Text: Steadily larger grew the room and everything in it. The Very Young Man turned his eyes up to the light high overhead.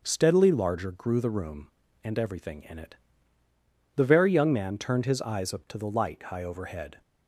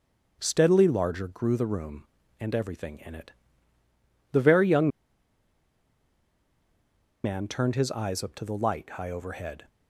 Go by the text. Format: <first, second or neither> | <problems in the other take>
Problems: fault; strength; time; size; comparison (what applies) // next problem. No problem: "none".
first | starts louder than the rest; until 1.4 s; 6.5 dB; also in the first // pauses between "Young" and "Man"; strong; at 4.8 s; 2.3 s long